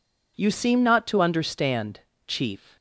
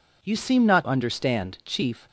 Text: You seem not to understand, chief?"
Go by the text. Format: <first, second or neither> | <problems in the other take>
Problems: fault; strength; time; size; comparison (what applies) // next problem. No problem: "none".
first | skips "to"; at 0.8 s